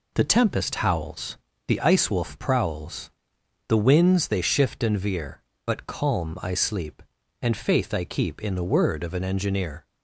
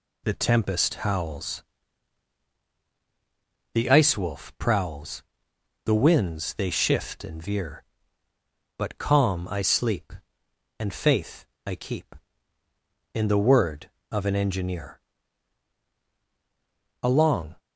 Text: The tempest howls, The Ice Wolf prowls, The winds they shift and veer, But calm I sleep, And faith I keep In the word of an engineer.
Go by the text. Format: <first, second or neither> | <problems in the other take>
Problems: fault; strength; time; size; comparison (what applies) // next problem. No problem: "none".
first | pauses between "faith" and "I"; slight; at 11.4 s; 0.22 s long // goes on to say "Along"; from 17.0 s on; 0.52 s long